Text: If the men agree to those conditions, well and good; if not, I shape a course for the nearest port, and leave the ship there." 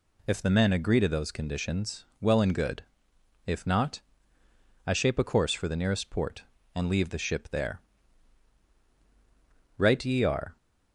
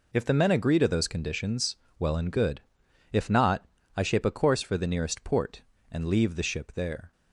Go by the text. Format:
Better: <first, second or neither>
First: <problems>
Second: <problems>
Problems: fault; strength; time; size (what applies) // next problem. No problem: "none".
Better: second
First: goes on to say "Right ye are"; noticeable; from 9.7 s on; 0.78 s long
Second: none